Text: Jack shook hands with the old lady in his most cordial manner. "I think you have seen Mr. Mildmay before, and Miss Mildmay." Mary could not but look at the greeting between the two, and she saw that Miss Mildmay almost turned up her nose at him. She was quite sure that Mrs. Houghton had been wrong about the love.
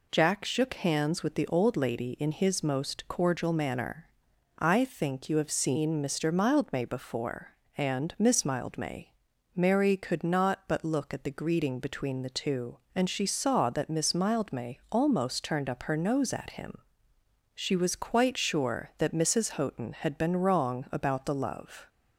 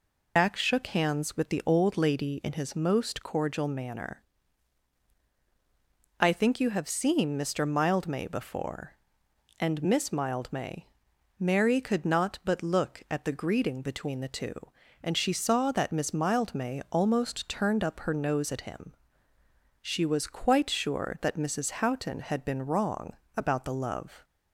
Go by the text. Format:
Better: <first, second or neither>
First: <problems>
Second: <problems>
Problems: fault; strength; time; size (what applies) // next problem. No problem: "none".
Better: first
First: none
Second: loses the start of "Jack"; at 0.3 s; 115 ms // pauses between "wrong" and "about"; slight; at 23.1 s; 0.20 s long